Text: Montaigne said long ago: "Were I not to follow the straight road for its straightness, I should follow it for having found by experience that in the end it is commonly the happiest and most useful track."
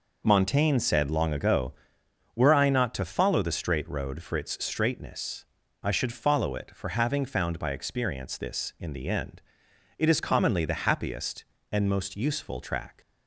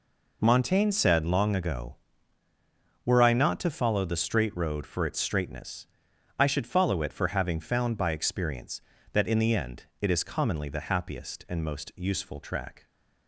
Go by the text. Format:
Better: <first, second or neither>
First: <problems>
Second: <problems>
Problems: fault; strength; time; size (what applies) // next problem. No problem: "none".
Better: second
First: says "this" for "that"; at 8.3 s // pauses between "end" and "it"; noticeable; at 9.4 s; 0.58 s long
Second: pauses between "end" and "it"; slight; at 9.8 s; 0.16 s long